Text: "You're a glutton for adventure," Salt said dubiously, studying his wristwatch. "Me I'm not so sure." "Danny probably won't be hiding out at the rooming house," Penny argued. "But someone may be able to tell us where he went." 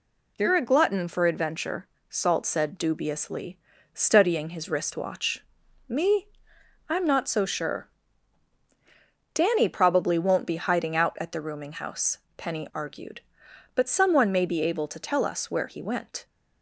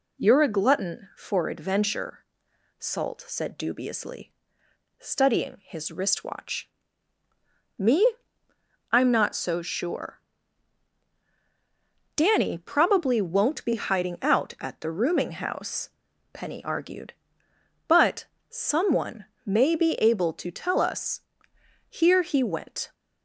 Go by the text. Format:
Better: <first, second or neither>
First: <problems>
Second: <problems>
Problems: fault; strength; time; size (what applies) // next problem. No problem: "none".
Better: first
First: pauses between "Me" and "I'm"; noticeable; at 6.2 s; 0.60 s long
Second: pauses between "Me" and "I'm"; noticeable; at 8.1 s; 0.76 s long // pauses between "But" and "someone"; slight; at 18.2 s; 0.24 s long // pauses between "someone" and "may"; slight; at 19.2 s; 0.20 s long // says "here" for "where"; at 21.8 s